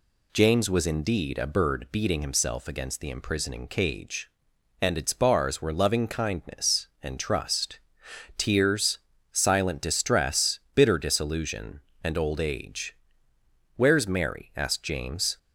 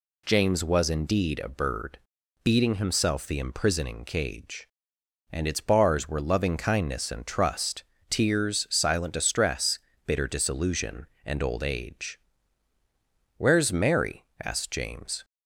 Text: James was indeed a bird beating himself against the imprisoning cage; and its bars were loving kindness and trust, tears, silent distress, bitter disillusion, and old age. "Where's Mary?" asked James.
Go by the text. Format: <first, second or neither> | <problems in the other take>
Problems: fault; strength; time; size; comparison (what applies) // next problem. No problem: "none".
first | pauses between "bird" and "beating"; noticeable; at 1.9 s; 0.46 s long // skips "against"; at 3.2 s